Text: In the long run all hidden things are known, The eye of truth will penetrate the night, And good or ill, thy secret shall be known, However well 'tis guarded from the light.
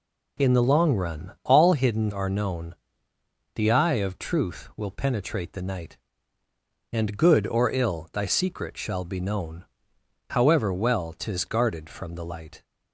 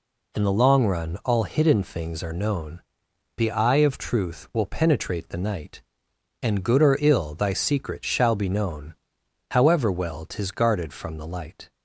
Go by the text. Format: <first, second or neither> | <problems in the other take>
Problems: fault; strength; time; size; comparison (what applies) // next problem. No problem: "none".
second | skips "things"; at 2.1 s